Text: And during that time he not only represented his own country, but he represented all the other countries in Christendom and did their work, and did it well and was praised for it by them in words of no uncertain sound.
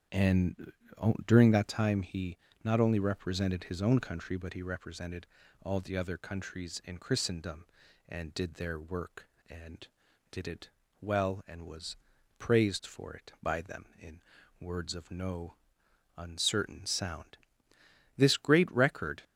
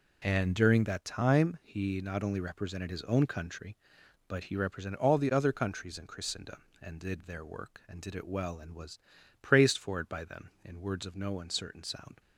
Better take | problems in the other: second | starts louder than the rest; strong; until 1.6 s; 9 dB // pauses between "And" and "during"; noticeable; at 0.7 s; 0.54 s long // pauses between "he" and "not"; slight; at 2.3 s; 0.26 s long // pauses between "represented" and "all"; slight; at 5.2 s; 0.36 s long // pauses between "it" and "well"; slight; at 10.6 s; 0.32 s long // pauses between "was" and "praised"; at 11.9 s; 0.42 s long; also in the second // pauses between "in" and "words"; at 14.2 s; 0.38 s long // pauses between "no" and "uncertain"; noticeable; at 15.5 s; 0.64 s long // goes on to say "This great record"; noticeable; from 18.1 s on; 1.0 s long

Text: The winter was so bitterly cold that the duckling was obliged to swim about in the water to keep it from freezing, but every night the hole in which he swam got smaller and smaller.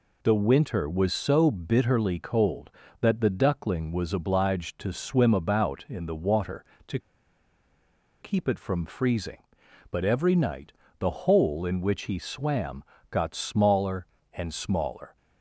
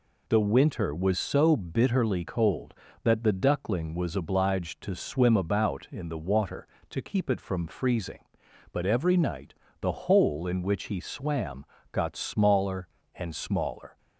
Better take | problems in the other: second | pauses between "to" and "keep"; at 6.9 s; 1.2 s long // pauses between "night" and "the"; slight; at 10.7 s; 0.28 s long; slight in the second // pauses between "swam" and "got"; slight; at 12.8 s; 0.26 s long; slight in the second

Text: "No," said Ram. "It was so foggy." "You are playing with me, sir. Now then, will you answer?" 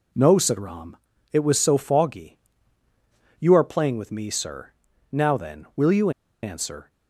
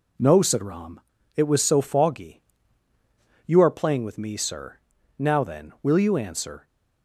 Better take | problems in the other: second | pauses between "you" and "answer"; slight; at 6.0 s; 0.33 s long

